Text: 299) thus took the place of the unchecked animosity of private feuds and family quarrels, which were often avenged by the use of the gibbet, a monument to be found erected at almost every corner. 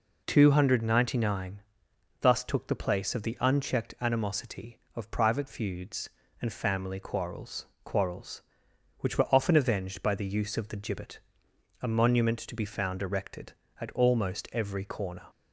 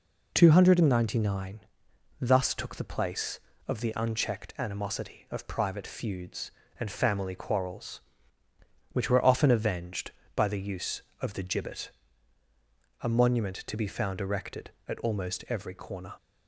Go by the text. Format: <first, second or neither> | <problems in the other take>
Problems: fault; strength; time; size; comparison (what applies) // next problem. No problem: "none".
second | says "quarrels" twice; at 7.8 s